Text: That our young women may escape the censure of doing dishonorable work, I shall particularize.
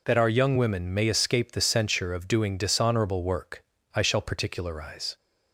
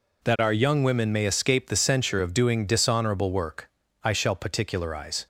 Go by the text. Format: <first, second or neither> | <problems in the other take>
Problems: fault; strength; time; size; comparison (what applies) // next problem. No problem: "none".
neither | none